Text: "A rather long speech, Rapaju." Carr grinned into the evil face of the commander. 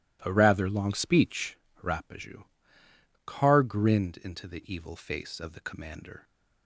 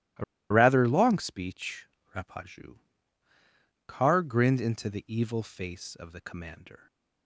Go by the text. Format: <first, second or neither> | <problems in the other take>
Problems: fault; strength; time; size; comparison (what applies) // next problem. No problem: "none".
first | pauses between "A" and "rather"; slight; at 0.2 s; 0.28 s long